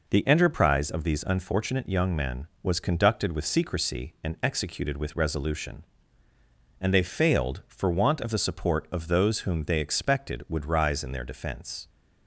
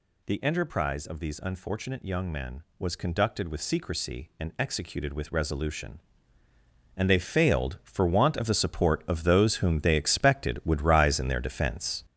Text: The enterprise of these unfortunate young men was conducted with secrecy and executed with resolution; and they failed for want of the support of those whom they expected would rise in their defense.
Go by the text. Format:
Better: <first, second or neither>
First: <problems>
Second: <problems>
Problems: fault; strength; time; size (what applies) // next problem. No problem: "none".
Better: first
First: none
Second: gets louder; strong; throughout; 7.5 dB